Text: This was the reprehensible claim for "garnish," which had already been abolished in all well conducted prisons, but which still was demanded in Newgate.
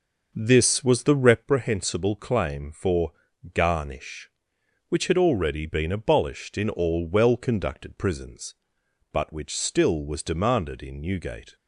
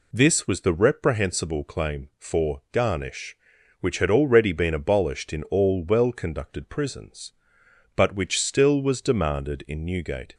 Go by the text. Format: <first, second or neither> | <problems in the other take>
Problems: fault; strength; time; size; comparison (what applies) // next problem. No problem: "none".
second | starts louder than the rest; noticeable; until 1.5 s; 6 dB // pauses between "for" and "garnish"; at 3.1 s; 0.42 s long